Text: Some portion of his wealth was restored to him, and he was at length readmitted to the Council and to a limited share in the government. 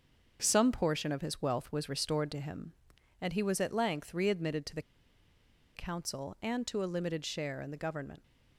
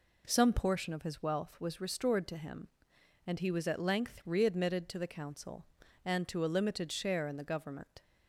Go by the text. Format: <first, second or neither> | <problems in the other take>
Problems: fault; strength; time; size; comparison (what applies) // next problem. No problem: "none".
second | starts louder than the rest; until 1.4 s; 6.5 dB // pauses between "the" and "Council"; noticeable; at 4.8 s; 0.94 s long